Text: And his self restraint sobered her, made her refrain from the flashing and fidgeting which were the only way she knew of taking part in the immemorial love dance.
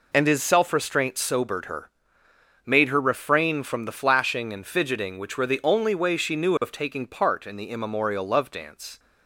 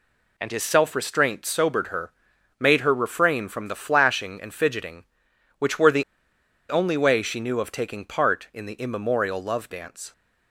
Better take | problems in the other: first | pauses between "the" and "only"; noticeable; at 6.0 s; 0.66 s long

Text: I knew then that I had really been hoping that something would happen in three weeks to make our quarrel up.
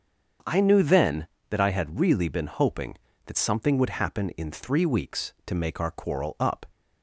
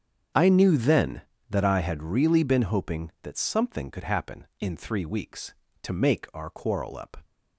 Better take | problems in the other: first | starts louder than the rest; strong; until 1.6 s; 8 dB; also in the first // says "could" for "would"; at 3.9 s

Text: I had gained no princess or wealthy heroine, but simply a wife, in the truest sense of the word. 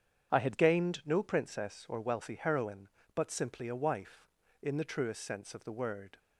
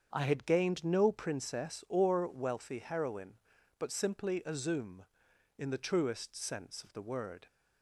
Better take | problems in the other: first | starts louder than the rest; strong; until 1.1 s; 7 dB; strong in the first // says "zoom" for "wife"; at 4.5 s

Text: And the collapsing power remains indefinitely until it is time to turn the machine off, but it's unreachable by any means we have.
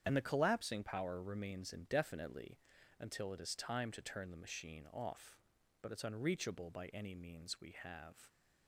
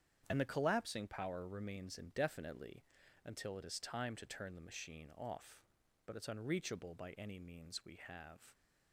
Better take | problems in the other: second | loses the start of "And"; at 0.0 s; 50 ms // starts louder than the rest; strong; until 1.0 s; 8.5 dB; strong in the second // pauses between "indefinitely" and "until"; at 2.5 s; 0.40 s long; also in the second

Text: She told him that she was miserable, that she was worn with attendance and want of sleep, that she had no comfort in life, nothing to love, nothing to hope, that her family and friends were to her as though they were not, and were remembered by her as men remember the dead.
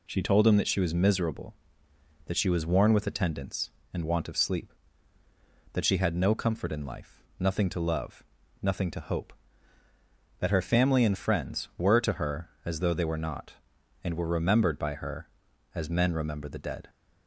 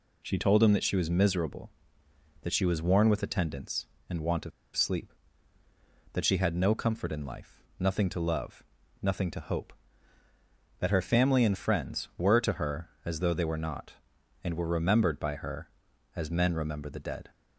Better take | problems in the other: first | pauses between "of" and "sleep"; slight; at 4.5 s; 0.25 s long

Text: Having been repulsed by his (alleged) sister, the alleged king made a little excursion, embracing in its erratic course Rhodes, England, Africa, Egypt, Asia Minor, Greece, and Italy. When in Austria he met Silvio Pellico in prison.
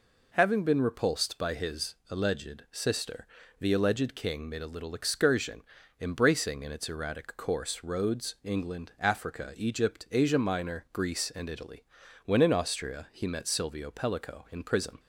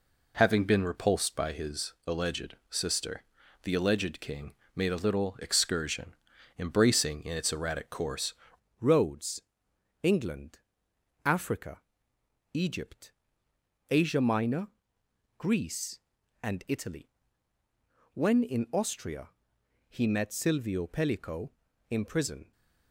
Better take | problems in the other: first | pauses between "king" and "made"; slight; at 4.5 s; 0.24 s long // changes voice at "Rhodes"; from 8.8 s on; 13.7 s long // pauses between "Austria" and "he"; noticeable; at 19.2 s; 0.58 s long

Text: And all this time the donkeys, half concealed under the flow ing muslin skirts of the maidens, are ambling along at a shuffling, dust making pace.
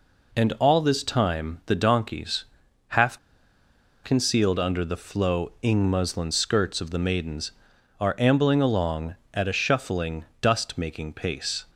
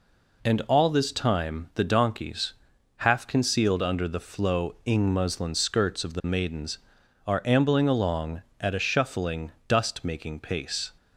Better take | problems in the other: second | pauses between "half" and "concealed"; noticeable; at 3.1 s; 0.85 s long

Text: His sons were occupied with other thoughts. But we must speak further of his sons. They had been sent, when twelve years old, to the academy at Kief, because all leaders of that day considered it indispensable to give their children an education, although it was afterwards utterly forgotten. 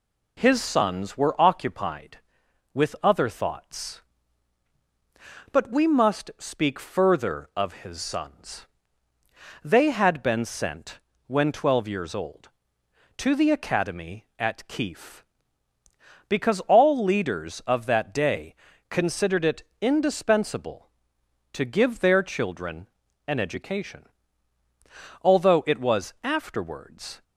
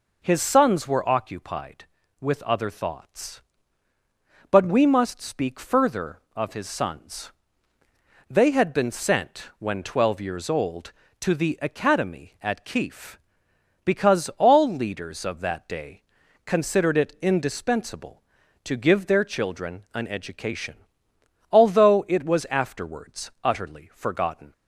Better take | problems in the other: second | pauses between "day" and "considered"; slight; at 18.5 s; 0.36 s long; also in the second // pauses between "it" and "indispensable"; slight; at 19.6 s; 0.16 s long // pauses between "children" and "an"; at 22.8 s; 0.40 s long // stops before "utterly forgotten"; at 27.2 s

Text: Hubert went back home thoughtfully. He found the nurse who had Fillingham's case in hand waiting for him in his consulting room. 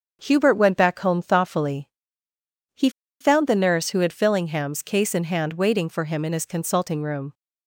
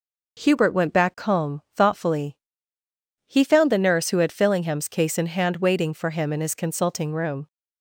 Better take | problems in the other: second | starts louder than the rest; strong; until 1.2 s; 7.5 dB // pauses between "He" and "found"; slight; at 2.8 s; 0.31 s long

